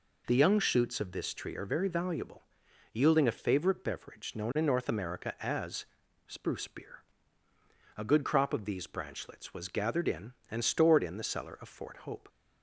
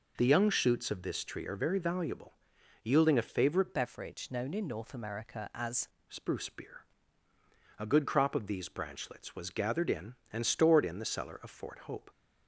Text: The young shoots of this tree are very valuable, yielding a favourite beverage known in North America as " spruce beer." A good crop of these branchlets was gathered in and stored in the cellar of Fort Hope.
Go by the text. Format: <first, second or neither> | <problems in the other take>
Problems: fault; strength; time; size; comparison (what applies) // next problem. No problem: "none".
first | changes voice from "beverage" to "as"; from 3.7 to 5.8 s; 2.1 s long